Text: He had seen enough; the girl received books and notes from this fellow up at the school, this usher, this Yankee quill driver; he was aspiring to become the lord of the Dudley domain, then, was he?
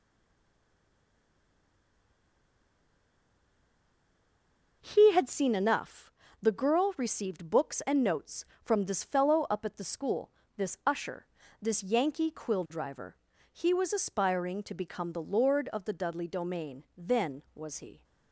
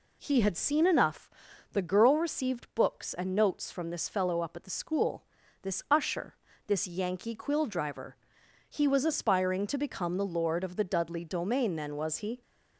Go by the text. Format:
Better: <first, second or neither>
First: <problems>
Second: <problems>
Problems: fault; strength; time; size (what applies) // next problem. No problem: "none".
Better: second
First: stays silent before the first word; strong; until 4.8 s; 4.8 s long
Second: none